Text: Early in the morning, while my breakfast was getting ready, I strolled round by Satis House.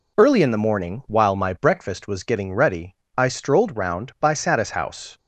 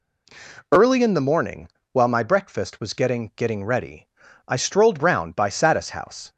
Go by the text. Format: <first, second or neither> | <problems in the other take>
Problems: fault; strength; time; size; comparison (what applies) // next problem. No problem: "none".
first | says "getting" twice; at 3.3 s